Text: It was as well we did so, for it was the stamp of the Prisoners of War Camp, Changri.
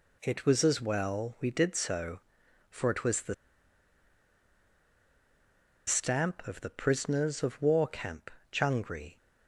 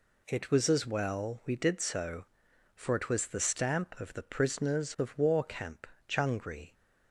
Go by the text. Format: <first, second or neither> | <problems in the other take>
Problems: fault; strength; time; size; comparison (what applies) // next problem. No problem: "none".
second | pauses between "the" and "stamp"; strong; at 3.3 s; 2.5 s long